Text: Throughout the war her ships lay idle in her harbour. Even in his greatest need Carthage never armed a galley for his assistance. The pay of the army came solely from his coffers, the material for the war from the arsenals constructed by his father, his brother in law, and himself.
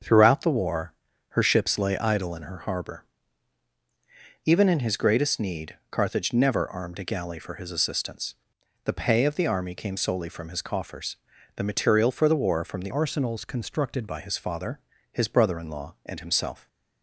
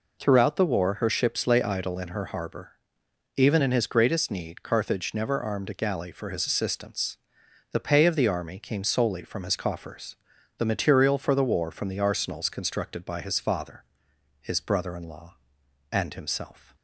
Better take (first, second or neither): second